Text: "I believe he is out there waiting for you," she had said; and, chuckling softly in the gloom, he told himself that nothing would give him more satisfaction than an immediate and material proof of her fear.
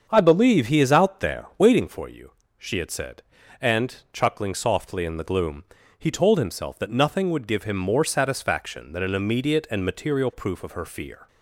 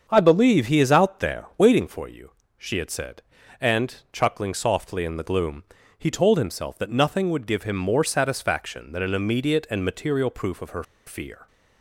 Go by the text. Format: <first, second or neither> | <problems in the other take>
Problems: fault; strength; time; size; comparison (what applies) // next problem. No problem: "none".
first | starts louder than the rest; until 1.0 s; 7 dB; also in the first // pauses between "her" and "fear"; slight; at 10.8 s; 0.23 s long